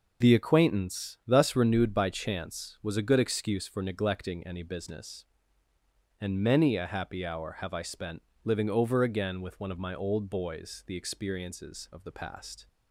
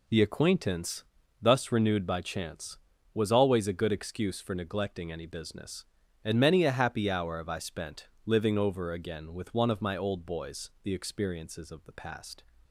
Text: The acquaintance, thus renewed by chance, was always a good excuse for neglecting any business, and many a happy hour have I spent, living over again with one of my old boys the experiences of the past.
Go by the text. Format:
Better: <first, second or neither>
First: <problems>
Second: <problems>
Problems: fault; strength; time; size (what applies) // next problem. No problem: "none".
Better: second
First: skips "always"; at 2.9 s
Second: none